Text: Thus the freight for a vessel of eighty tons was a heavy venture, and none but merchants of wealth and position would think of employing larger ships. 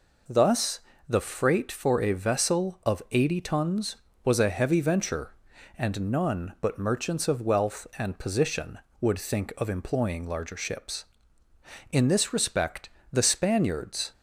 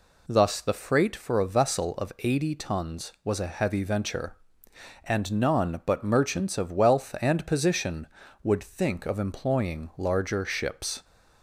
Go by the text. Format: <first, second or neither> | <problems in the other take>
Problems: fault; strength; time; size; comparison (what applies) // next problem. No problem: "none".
second | pauses between "Thus" and "the"; slight; at 0.7 s; 0.28 s long // goes on to say "In this respect the Spaniards"; strong; from 11.9 s on; 2.2 s long